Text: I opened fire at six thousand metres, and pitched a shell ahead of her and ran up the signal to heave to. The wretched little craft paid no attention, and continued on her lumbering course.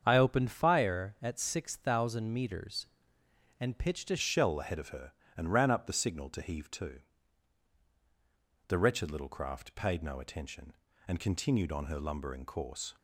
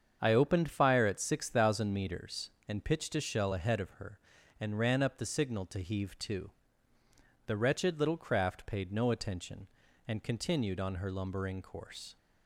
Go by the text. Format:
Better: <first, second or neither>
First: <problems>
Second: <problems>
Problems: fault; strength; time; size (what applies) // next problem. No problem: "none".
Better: second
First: starts louder than the rest; strong; until 1.0 s; 7 dB // changes voice at "shell"; from 4.1 s on; 8.8 s long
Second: starts louder than the rest; strong; until 1.2 s; 7.5 dB